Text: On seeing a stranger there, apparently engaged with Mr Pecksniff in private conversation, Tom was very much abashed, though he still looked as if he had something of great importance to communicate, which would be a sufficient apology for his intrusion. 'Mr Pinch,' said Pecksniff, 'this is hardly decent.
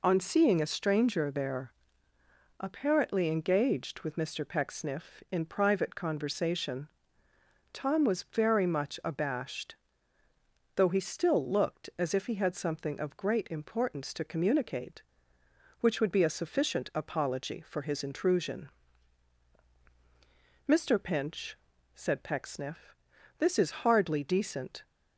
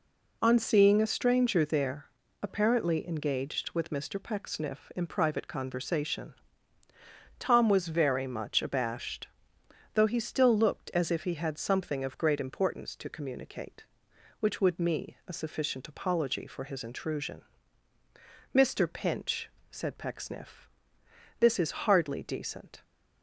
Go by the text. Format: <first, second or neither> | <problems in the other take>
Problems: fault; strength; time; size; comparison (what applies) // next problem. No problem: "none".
first | says "me" for "be"; at 14.7 s